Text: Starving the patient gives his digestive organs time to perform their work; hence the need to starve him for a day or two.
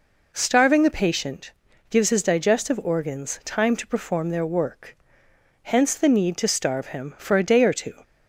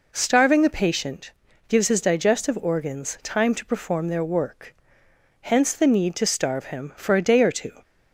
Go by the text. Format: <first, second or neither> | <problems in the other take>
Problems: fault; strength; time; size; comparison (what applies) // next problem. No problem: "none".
neither | pauses between "patient" and "gives"; slight; the same in both